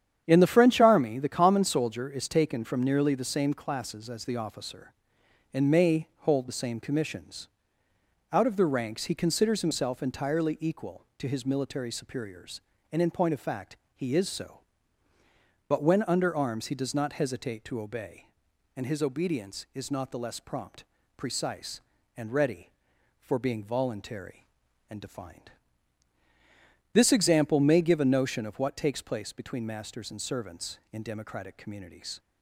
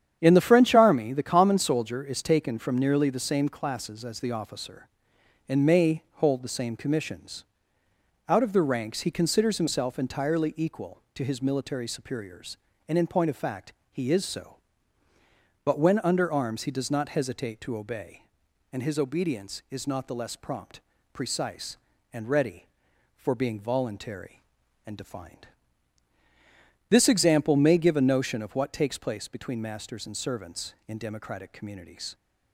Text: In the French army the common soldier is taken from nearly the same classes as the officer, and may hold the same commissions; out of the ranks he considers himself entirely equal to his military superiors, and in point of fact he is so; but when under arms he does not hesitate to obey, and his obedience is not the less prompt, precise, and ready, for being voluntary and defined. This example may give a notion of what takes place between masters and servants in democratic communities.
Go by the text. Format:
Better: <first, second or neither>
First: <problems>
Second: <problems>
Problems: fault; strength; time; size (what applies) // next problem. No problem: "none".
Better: neither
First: starts louder than the rest; strong; until 1.2 s; 9 dB // pauses between "fact" and "he"; slight; at 13.7 s; 0.18 s long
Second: starts louder than the rest; strong; until 1.2 s; 9 dB // pauses between "fact" and "he"; slight; at 13.7 s; 0.18 s long